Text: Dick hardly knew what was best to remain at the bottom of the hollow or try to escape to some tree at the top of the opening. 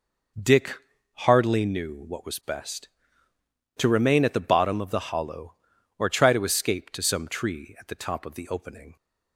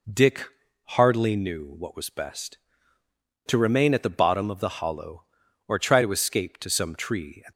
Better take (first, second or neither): first